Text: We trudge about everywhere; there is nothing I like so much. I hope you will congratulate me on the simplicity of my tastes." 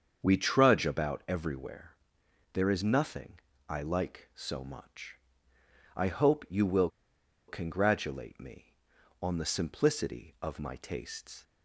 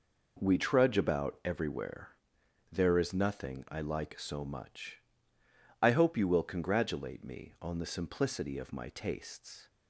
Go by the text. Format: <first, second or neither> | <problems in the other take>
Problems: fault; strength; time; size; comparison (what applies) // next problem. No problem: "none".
second | starts louder than the rest; until 1.2 s; 7 dB // pauses between "nothing" and "I"; slight; at 3.3 s; 0.28 s long // pauses between "will" and "congratulate"; noticeable; at 6.8 s; 0.58 s long